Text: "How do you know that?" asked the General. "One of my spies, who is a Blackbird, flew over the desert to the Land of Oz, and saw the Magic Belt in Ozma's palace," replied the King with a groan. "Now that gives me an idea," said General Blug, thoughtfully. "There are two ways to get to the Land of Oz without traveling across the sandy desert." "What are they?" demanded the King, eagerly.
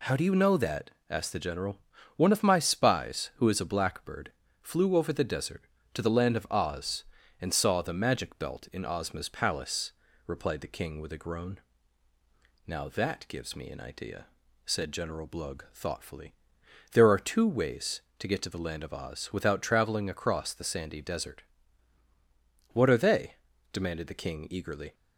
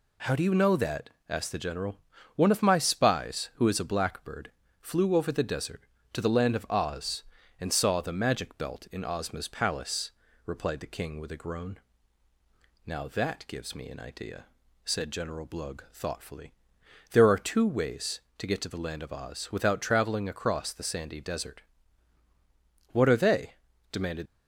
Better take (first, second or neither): first